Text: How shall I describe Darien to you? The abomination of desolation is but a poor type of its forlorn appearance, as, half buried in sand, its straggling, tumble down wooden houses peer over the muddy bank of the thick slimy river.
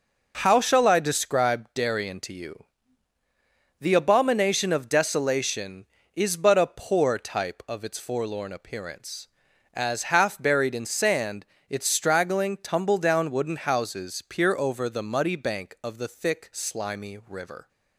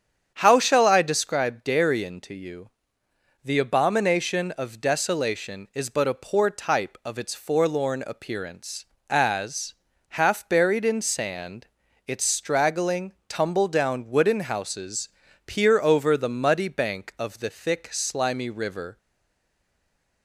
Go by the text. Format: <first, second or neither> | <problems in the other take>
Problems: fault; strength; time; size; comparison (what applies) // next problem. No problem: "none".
first | starts louder than the rest; strong; until 1.3 s; 8 dB // pauses between "houses" and "peer"; at 15.0 s; 0.38 s long // stays silent after the last word; noticeable; from 18.9 s on; 1.3 s long